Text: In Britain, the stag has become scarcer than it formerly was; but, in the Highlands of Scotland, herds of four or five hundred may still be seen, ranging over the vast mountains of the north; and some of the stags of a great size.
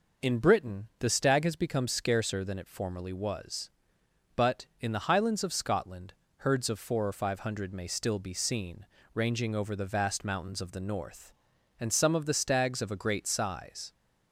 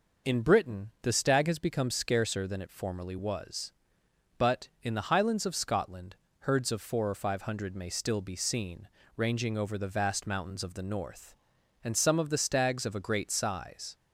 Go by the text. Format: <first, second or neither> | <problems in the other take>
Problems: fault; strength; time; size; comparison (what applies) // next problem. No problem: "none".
neither | none